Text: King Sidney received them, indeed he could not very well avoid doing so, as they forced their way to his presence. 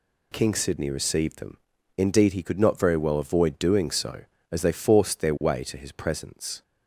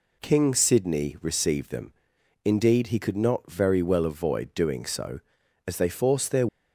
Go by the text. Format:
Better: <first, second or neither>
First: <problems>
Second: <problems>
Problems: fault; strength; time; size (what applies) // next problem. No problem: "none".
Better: first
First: none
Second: stops before "way to his presence"; at 6.4 s